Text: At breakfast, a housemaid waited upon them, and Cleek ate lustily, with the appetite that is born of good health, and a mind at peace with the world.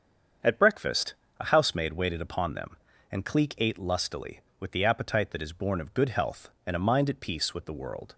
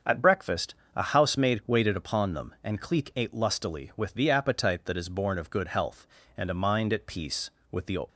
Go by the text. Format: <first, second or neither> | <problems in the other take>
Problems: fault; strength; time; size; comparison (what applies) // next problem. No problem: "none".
first | starts louder than the rest; until 1.2 s; 7 dB; strong in the first // stops before "world"; at 8.0 s